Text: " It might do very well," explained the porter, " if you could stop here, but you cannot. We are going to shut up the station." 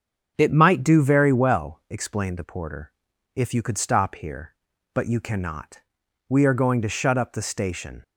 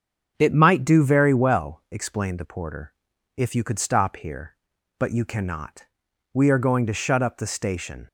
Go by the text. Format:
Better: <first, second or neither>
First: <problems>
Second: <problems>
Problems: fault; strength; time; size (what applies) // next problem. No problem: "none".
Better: neither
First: starts louder than the rest; strong; until 1.3 s; 7.5 dB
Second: starts louder than the rest; strong; until 1.3 s; 7.5 dB